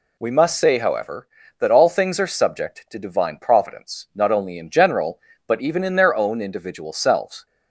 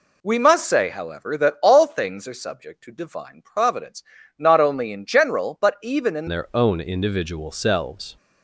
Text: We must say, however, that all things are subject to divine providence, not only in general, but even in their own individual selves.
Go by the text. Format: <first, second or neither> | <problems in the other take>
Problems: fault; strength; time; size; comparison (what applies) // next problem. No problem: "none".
first | changes voice at "their"; from 6.2 s on; 1.9 s long